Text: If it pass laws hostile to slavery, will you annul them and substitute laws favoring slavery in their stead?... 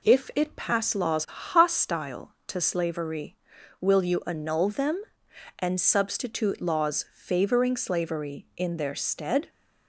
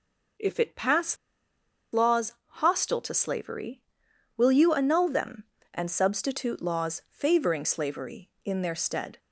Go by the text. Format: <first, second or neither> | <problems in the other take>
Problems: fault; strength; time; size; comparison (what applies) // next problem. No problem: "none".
first | pauses between "pass" and "laws"; noticeable; at 1.1 s; 0.76 s long